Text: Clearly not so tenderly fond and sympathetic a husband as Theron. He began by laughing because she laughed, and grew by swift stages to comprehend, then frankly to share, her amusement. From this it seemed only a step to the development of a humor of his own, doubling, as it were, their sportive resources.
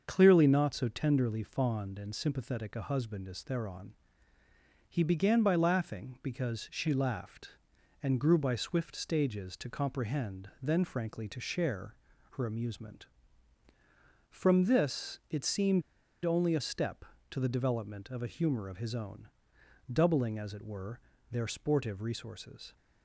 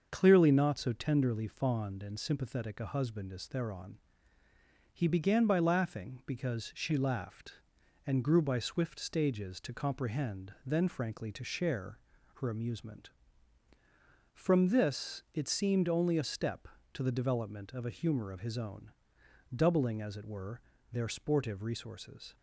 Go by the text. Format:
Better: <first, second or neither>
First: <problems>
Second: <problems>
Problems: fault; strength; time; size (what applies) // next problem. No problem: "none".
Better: second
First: starts louder than the rest; until 1.0 s; 6.5 dB // pauses between "seemed" and "only"; at 15.8 s; 0.43 s long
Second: starts louder than the rest; until 1.1 s; 6.5 dB